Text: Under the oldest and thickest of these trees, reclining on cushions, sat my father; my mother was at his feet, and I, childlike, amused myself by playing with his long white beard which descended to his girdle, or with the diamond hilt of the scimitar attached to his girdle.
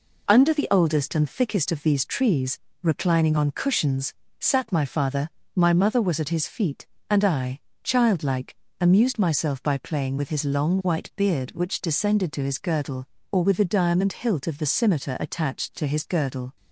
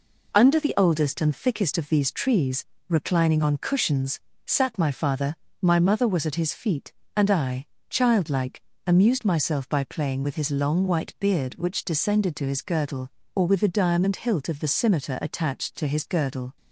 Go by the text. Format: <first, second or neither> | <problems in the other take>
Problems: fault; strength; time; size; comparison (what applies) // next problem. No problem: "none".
neither | none